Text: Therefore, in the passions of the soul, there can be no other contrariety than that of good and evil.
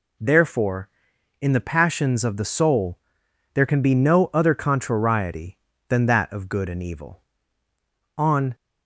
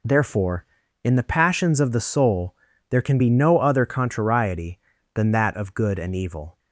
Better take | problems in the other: second | goes on to say "On"; slight; from 8.1 s on; 0.38 s long

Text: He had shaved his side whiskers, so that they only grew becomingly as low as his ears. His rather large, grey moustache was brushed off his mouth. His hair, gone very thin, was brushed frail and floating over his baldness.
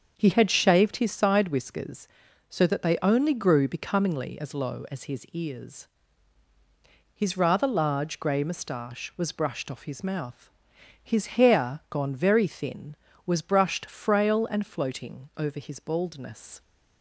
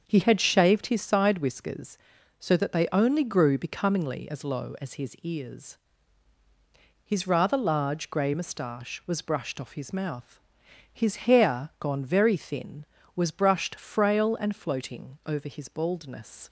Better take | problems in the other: neither | starts louder than the rest; the same in both

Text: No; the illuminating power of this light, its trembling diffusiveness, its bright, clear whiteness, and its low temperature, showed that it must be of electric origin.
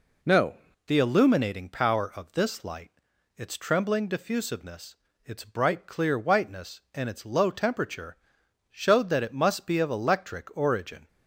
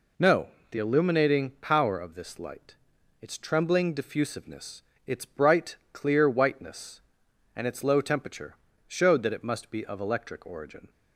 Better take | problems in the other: second | changes voice at "the"; from 0.8 s on; 10.2 s long

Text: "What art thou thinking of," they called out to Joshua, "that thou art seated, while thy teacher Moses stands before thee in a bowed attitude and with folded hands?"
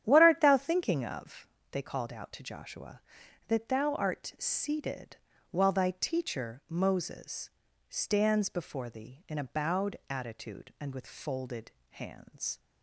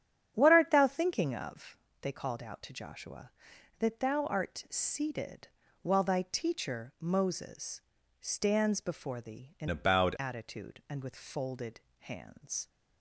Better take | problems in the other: first | starts louder than the rest; strong; until 1.3 s; 8.5 dB; strong in the first // pauses between "Moses" and "stands"; at 7.7 s; 0.40 s long; also in the first // changes voice from "a" to "bowed"; from 9.6 to 10.1 s; 0.5 s long // pauses between "folded" and "hands"; slight; at 11.8 s; 0.20 s long; slight in the first

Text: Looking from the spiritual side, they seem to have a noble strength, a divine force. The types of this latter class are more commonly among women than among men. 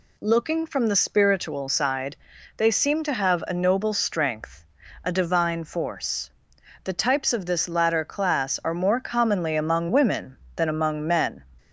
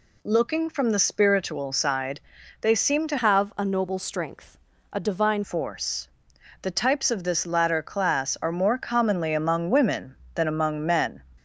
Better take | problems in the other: first | changes voice from "have" to "divine"; from 3.1 to 5.4 s; 2.3 s long

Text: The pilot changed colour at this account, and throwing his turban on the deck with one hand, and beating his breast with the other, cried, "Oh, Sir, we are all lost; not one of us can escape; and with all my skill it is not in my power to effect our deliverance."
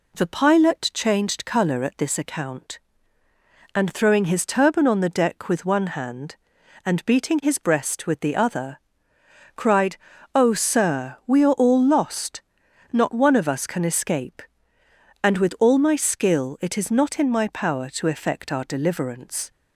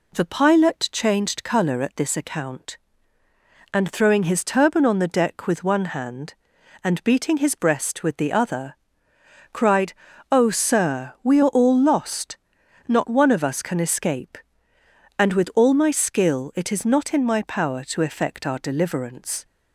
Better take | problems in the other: neither | none

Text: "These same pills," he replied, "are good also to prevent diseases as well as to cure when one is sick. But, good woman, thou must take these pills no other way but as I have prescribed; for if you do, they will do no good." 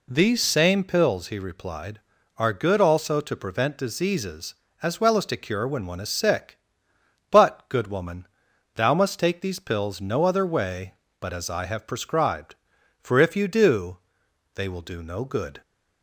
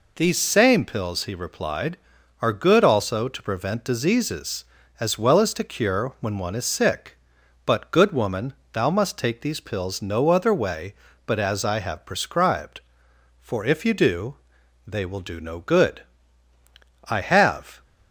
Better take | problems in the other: first | goes on to say "I have"; noticeable; from 17.0 s on; 0.76 s long

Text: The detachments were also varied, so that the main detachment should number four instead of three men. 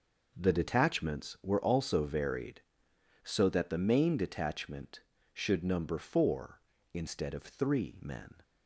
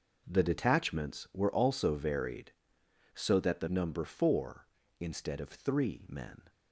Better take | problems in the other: first | skips "main detachment should"; at 3.6 s

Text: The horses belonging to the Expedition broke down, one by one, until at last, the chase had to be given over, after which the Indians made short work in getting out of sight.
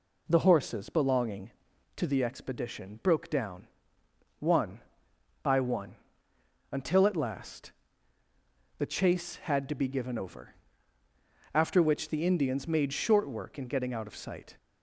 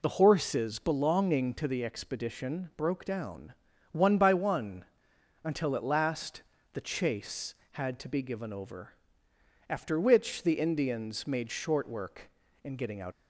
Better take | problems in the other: first | stops before "of sight"; at 13.1 s

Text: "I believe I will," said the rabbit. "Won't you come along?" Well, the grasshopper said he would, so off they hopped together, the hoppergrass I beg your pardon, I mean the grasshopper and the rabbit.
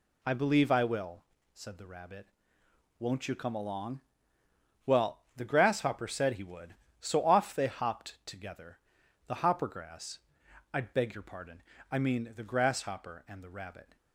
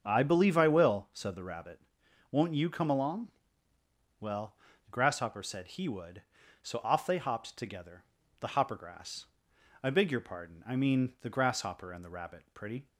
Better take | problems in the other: first | starts louder than the rest; until 1.0 s; 7 dB // pauses between "hoppergrass" and "I"; noticeable; at 9.2 s; 0.58 s long; noticeable in the first // goes on to say "Pretty"; slight; from 12.5 s on; 0.32 s long

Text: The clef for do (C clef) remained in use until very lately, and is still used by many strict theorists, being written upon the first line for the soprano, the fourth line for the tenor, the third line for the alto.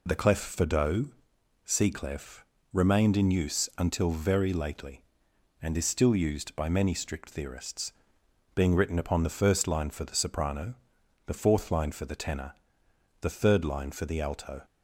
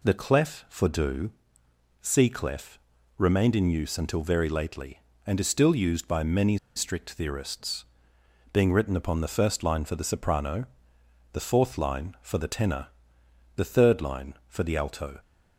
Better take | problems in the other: first | pauses between "many" and "strict"; slight; at 6.5 s; 0.19 s long

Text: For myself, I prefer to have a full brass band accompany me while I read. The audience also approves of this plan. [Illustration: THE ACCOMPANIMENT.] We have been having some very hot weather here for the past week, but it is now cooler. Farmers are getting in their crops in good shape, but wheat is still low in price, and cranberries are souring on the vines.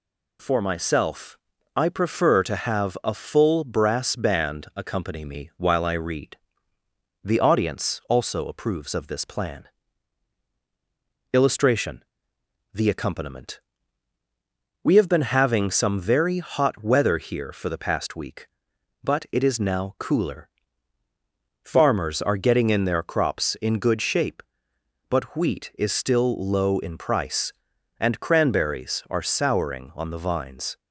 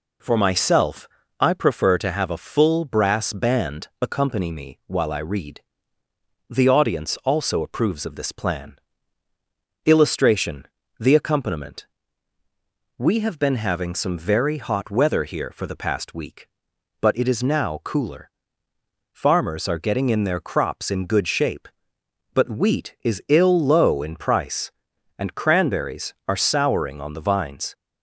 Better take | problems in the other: first | pauses between "band" and "accompany"; slight; at 3.8 s; 0.16 s long // says "ill" for "still"; at 23.2 s

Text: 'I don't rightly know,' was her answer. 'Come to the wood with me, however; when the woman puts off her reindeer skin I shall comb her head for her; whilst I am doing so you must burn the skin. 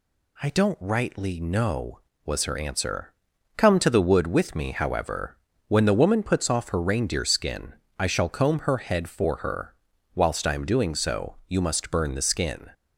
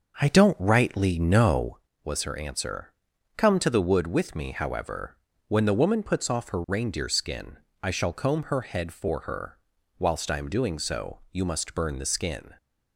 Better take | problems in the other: first | starts louder than the rest; until 1.8 s; 6 dB // pauses between "skin" and "I"; slight; at 7.5 s; 0.26 s long; slight in the first

